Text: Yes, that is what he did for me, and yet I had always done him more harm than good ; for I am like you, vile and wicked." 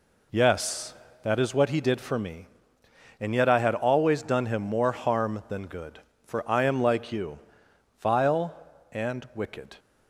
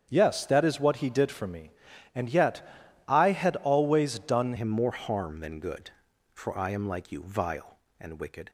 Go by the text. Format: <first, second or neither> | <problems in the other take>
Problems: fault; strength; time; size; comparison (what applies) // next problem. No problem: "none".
first | starts louder than the rest; strong; until 1.1 s; 8 dB // pauses between "yet" and "I"; at 2.6 s; 0.44 s long // changes voice at "him"; from 4.5 s on; 3.9 s long